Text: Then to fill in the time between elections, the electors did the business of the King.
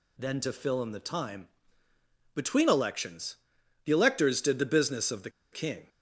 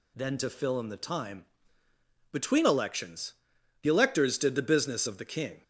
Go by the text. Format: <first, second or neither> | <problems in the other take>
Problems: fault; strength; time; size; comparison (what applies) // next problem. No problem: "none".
second | pauses between "time" and "between"; noticeable; at 1.4 s; 0.86 s long; noticeable in the second // pauses between "the" and "King"; slight; at 5.2 s; 0.22 s long